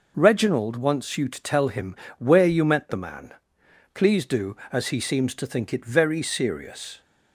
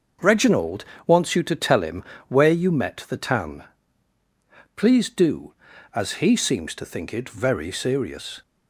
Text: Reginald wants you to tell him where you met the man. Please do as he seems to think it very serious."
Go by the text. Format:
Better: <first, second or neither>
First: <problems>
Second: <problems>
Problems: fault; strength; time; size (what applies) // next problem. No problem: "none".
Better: first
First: pauses between "him" and "where"; slight; at 1.9 s; 0.22 s long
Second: starts louder than the rest; until 1.4 s; 6.5 dB // pauses between "Reginald" and "wants"; slight; at 0.8 s; 0.20 s long // pauses between "him" and "where"; slight; at 2.0 s; 0.28 s long // says "tan" for "man"; at 3.1 s